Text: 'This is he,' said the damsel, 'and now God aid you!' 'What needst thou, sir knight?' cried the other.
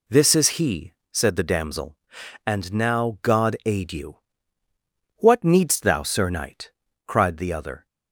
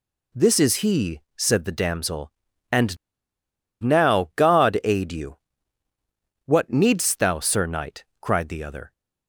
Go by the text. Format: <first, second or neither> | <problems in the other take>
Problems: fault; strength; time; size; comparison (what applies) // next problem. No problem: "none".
first | pauses between "and" and "now"; noticeable; at 2.9 s; 0.85 s long